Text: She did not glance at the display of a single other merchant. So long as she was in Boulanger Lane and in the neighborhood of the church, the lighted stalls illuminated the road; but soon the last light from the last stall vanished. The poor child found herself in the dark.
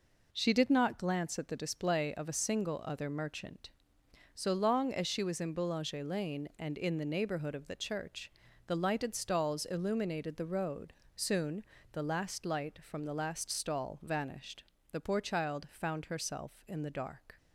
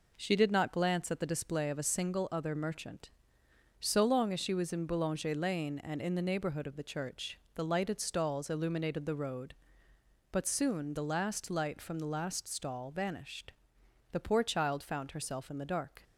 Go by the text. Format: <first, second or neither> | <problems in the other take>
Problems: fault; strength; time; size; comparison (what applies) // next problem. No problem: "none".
second | skips "but"; at 11.0 s // pauses between "soon" and "the"; slight; at 11.6 s; 0.30 s long